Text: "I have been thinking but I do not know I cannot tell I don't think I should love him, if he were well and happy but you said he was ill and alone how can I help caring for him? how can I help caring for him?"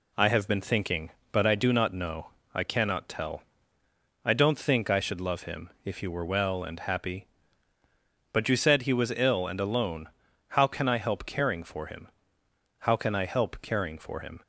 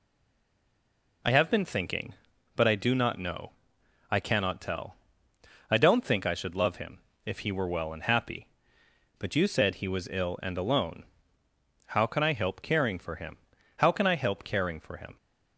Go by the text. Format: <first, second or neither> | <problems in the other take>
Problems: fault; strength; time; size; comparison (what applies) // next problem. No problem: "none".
first | stays silent before the first word; noticeable; until 1.2 s; 1.2 s long // pauses between "know" and "I"; noticeable; at 3.5 s; 0.58 s long; slight in the first // pauses between "tell" and "I"; noticeable; at 4.9 s; 0.74 s long; noticeable in the first // pauses between "alone" and "how"; noticeable; at 11.0 s; 0.82 s long; also in the first